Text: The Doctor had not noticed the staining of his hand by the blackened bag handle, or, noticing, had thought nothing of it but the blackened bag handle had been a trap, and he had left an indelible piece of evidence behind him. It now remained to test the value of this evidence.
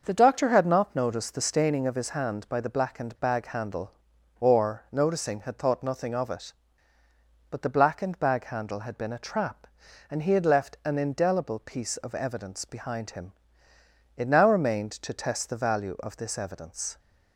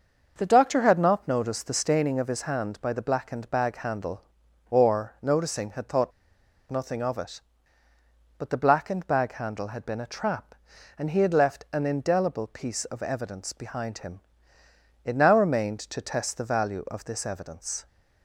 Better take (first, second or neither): first